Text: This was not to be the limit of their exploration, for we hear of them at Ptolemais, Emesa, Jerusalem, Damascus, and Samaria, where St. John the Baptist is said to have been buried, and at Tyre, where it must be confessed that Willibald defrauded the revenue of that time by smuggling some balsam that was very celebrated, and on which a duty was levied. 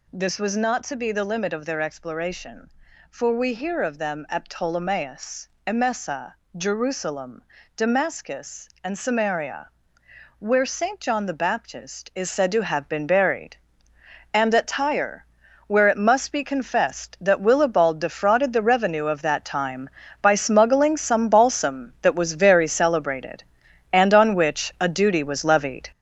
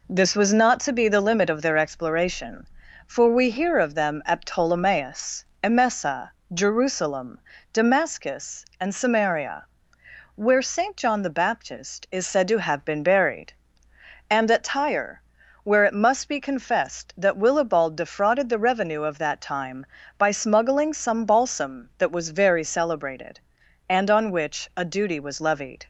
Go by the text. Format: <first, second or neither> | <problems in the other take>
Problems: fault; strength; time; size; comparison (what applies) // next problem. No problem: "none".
second | gets louder; throughout; 7 dB